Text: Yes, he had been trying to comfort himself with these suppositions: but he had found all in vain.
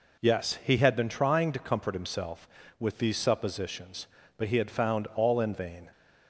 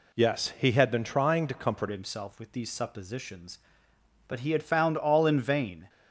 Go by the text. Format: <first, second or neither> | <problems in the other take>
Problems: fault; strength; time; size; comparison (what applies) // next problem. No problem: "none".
first | changes voice at "himself"; from 1.9 s on; 3.9 s long